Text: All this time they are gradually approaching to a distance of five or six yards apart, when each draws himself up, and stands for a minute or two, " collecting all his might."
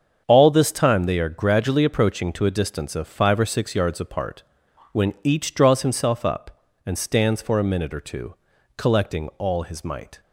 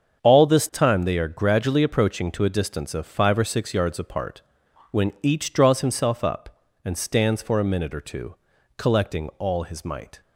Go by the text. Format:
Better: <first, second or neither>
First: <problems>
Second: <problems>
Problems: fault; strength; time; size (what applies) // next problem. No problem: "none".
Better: neither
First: starts louder than the rest; strong; until 1.2 s; 7 dB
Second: starts louder than the rest; strong; until 1.2 s; 7.5 dB